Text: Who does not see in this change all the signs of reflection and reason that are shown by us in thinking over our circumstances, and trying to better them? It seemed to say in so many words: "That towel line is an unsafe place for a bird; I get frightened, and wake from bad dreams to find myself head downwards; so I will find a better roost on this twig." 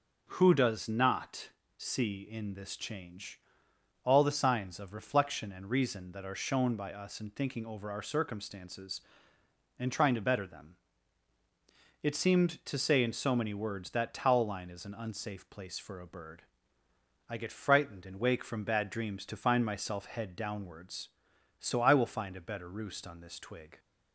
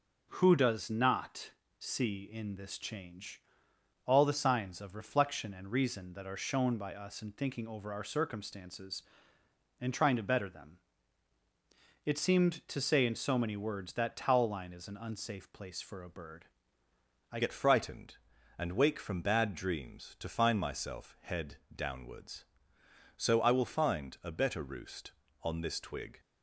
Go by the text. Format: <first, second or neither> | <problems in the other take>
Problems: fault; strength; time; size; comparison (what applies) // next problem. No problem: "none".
first | pauses between "not" and "see"; slight; at 1.5 s; 0.28 s long; slight in the first // pauses between "change" and "all"; noticeable; at 3.4 s; 0.64 s long; noticeable in the first // changes voice at "get"; from 17.3 s on; 8.8 s long // pauses between "head" and "downwards"; slight; at 21.5 s; 0.18 s long